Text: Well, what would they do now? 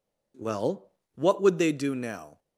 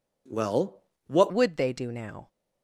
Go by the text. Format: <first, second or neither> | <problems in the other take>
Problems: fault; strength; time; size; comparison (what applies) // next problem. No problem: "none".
first | changes voice at "would"; from 1.2 s on; 1.0 s long